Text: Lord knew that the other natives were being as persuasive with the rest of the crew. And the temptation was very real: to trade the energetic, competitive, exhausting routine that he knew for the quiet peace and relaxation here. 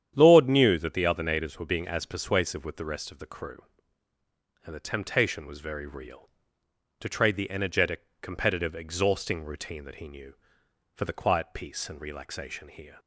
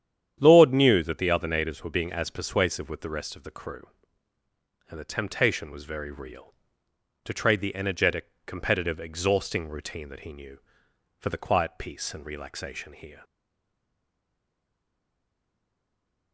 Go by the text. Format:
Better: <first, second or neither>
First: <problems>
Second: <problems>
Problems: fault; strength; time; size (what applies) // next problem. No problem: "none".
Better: first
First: starts louder than the rest; strong; until 1.1 s; 9.5 dB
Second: starts louder than the rest; strong; until 1.4 s; 9.5 dB // stays silent after the last word; strong; from 13.2 s on; 3.1 s long